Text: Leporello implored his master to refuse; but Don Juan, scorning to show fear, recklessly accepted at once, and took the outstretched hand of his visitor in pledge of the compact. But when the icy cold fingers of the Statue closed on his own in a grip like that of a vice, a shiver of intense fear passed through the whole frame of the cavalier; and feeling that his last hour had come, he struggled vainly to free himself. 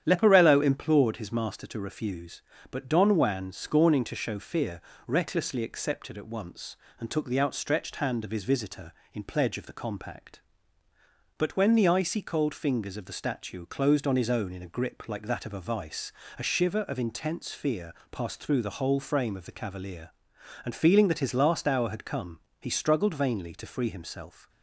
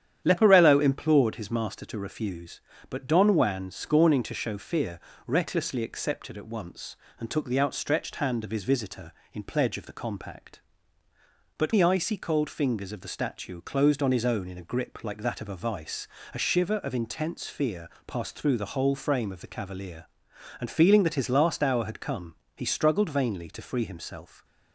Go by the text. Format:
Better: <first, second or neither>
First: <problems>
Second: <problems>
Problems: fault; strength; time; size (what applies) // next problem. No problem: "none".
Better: first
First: starts louder than the rest; strong; until 1.0 s; 9.5 dB // pauses between "fear" and "passed"; slight; at 17.9 s; 0.20 s long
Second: starts louder than the rest; strong; until 1.2 s; 9.5 dB // skips "when"; at 11.7 s // pauses between "fear" and "passed"; slight; at 17.8 s; 0.20 s long